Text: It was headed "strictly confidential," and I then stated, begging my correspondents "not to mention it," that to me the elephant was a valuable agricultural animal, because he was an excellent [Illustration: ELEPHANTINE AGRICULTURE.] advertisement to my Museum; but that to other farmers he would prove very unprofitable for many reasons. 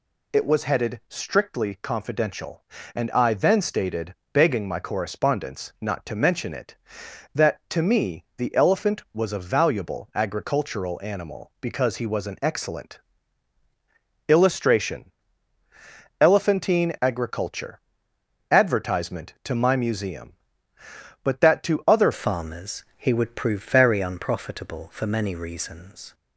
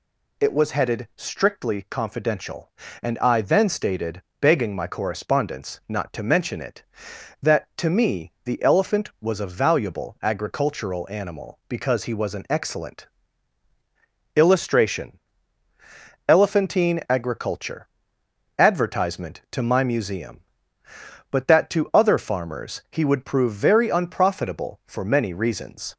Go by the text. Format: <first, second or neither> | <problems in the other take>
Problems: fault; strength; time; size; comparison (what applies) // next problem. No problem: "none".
second | pauses between "excellent" and "Illustration"; strong; at 12.9 s; 1.2 s long; strong in the second // changes voice at "farmers"; from 22.1 s on; 4.0 s long